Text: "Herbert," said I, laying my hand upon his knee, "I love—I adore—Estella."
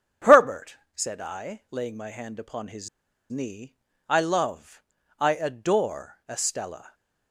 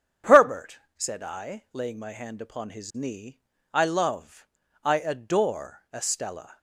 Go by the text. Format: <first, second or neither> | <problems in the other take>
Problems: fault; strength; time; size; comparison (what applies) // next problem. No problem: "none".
second | starts louder than the rest; strong; until 1.4 s; 8.5 dB; strong in the second // pauses between "his" and "knee"; at 2.8 s; 0.41 s long